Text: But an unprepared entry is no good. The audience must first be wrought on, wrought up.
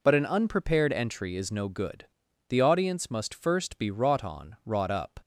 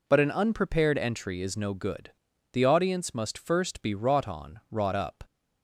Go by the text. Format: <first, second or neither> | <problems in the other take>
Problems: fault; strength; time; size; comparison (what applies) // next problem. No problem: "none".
neither | none